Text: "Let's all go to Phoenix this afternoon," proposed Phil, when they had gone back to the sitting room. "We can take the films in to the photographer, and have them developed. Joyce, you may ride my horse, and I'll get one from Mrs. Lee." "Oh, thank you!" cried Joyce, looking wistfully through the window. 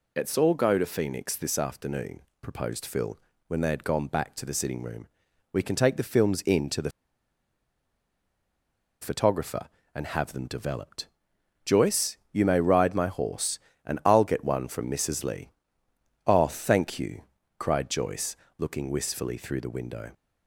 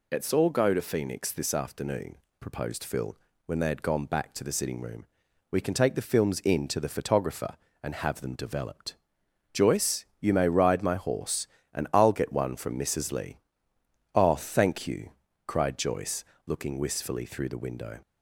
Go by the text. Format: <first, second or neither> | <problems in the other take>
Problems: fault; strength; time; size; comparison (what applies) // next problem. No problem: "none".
second | pauses between "the" and "photographer"; strong; at 6.8 s; 2.1 s long